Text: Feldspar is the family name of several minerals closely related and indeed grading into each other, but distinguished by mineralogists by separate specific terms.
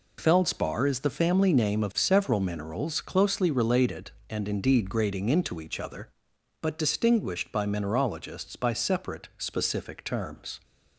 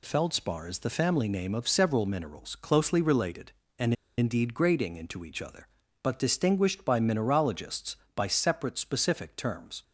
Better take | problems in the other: first | pauses between "and" and "indeed"; slight; at 3.9 s; 0.24 s long

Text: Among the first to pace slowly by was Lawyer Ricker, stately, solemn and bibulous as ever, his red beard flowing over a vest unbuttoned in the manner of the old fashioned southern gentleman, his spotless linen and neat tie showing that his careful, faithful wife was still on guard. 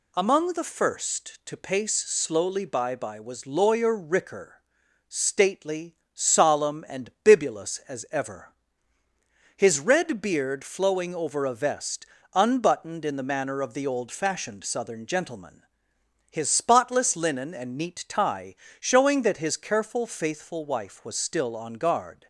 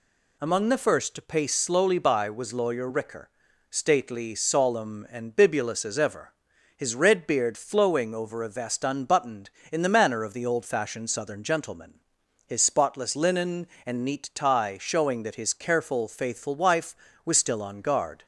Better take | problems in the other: second | says "by" twice; at 2.9 s // pauses between "vest" and "unbuttoned"; slight; at 12.0 s; 0.30 s long // pauses between "tie" and "showing"; slight; at 18.5 s; 0.26 s long

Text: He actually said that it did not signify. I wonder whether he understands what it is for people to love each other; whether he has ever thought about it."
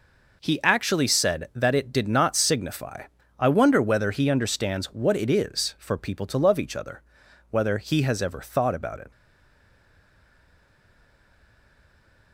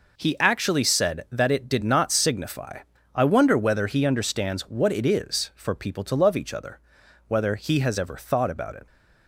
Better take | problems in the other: second | stays silent after the last word; strong; from 9.1 s on; 3.2 s long

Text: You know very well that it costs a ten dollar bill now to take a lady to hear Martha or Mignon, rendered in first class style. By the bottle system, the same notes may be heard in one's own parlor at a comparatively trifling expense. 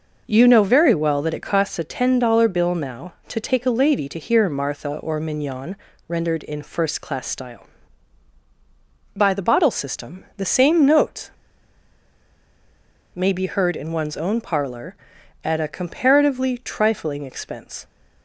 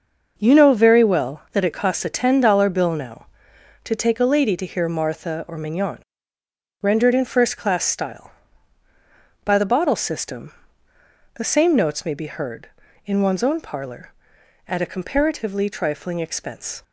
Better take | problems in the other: second | pauses between "notes" and "may"; strong; at 11.3 s; 1.8 s long

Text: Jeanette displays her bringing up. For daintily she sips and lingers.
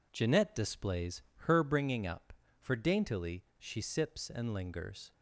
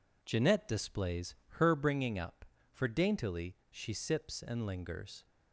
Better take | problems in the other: neither | pauses between "displays" and "her"; slight; the same in both // pauses between "daintily" and "she"; slight; the same in both

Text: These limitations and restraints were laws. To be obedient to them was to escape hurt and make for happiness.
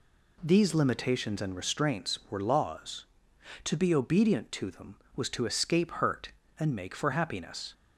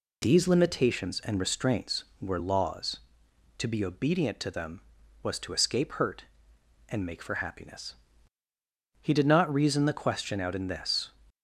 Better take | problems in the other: first | goes on to say "He did not reason the question out in this"; strong; from 9.0 s on; 2.1 s long

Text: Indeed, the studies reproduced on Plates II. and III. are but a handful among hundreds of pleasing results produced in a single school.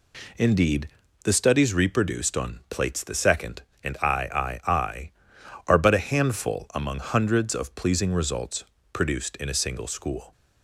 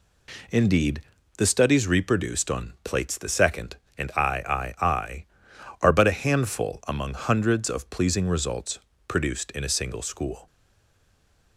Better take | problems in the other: first | pauses between "results" and "produced"; slight; at 8.7 s; 0.30 s long; slight in the first // stays silent after the last word; from 10.4 s on; 1.1 s long

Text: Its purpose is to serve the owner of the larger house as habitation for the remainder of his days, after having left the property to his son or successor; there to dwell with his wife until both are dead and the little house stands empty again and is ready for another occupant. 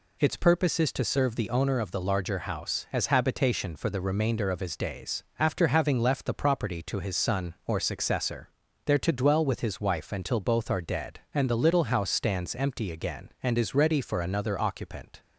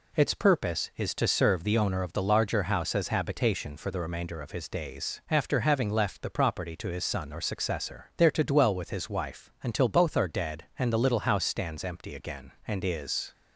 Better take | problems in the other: first | stops before "ready for another occupant"; at 13.3 s

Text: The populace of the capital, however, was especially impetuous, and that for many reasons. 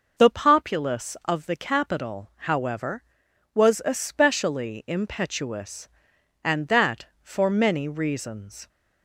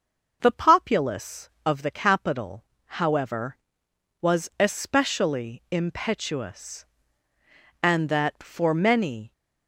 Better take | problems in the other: first | stops before "reasons"; at 9.3 s

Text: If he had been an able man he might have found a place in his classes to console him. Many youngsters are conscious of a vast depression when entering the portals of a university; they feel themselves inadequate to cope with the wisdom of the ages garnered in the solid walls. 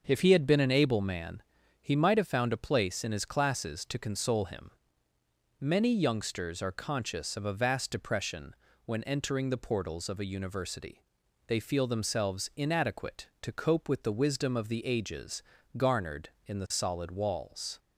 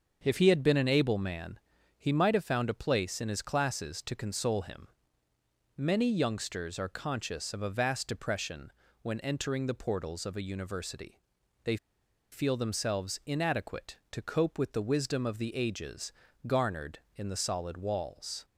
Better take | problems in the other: first | starts louder than the rest; until 1.2 s; 6.5 dB; also in the first // pauses between "man" and "he"; at 1.5 s; 0.40 s long; also in the first // pauses between "depression" and "when"; slight; at 8.7 s; 0.30 s long; slight in the first // pauses between "they" and "feel"; noticeable; at 11.7 s; 0.55 s long // pauses between "ages" and "garnered"; slight; at 16.1 s; 0.34 s long; slight in the first

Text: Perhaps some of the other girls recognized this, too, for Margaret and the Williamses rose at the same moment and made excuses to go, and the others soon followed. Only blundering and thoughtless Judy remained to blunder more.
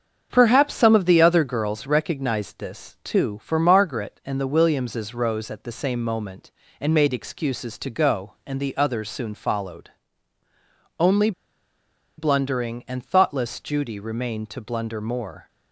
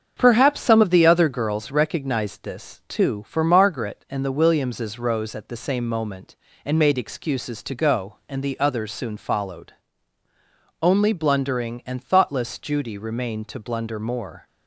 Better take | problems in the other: second | starts louder than the rest; strong; until 1.3 s; 7 dB; also in the second // pauses between "Only" and "blundering"; noticeable; at 11.3 s; 0.86 s long

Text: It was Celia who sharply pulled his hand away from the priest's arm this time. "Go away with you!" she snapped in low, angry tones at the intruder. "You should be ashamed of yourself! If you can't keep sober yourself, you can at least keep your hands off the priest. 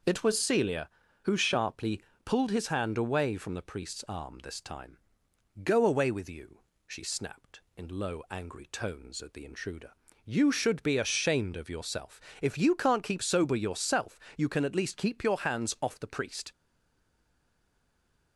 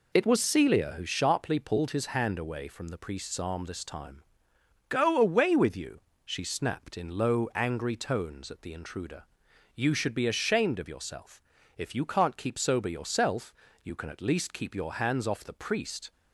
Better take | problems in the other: second | pauses between "sharply" and "pulled"; slight; at 2.0 s; 0.24 s long // stays silent after the last word; noticeable; from 16.5 s on; 1.8 s long

